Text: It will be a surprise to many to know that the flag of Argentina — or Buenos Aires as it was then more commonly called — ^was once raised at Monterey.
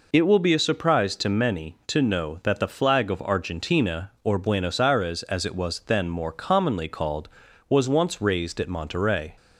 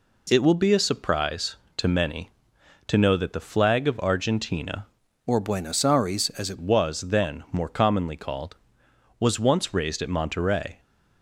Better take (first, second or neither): first